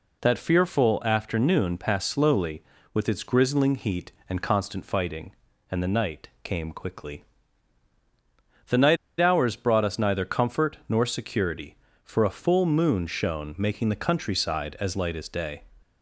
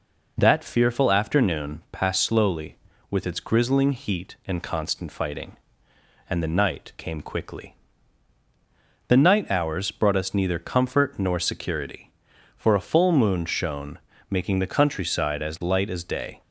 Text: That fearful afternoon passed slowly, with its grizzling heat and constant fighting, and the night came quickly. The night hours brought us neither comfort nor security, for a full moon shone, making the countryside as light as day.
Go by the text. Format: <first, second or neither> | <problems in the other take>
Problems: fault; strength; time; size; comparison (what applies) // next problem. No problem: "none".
second | pauses between "night" and "hours"; slight; at 8.9 s; 0.24 s long